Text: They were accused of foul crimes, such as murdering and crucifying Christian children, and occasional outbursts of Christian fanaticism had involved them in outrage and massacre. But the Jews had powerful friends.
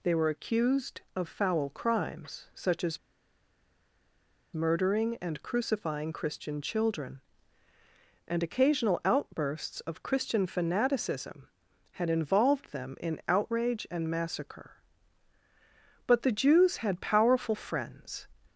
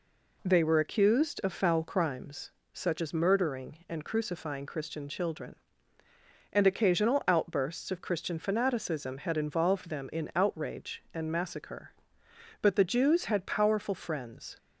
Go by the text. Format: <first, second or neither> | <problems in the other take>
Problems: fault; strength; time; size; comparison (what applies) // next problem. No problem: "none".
second | pauses between "as" and "murdering"; strong; at 2.9 s; 1.5 s long